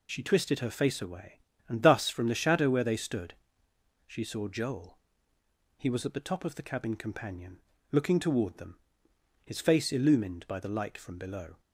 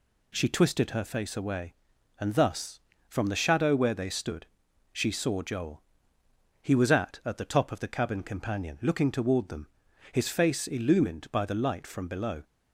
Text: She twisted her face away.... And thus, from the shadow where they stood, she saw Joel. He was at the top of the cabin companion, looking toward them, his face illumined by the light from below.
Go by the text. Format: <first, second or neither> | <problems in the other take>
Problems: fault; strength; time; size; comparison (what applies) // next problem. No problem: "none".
first | says "at" twice; at 7.2 s